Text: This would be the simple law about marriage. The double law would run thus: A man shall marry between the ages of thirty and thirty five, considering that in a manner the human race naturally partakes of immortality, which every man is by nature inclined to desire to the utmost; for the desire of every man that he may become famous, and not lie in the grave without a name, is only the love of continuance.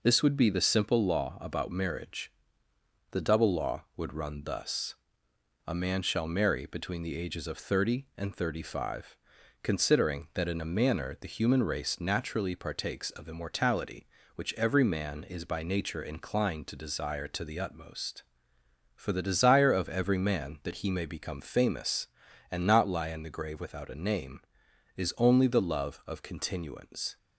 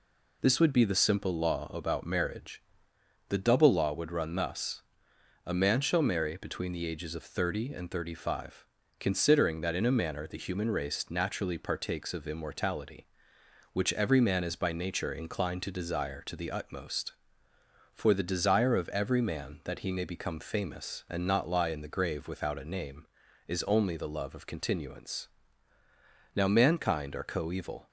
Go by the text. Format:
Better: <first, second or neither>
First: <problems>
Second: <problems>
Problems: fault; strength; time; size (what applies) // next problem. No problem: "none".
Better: first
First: none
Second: goes on to say "Now mankind are coeval"; from 26.3 s on; 1.5 s long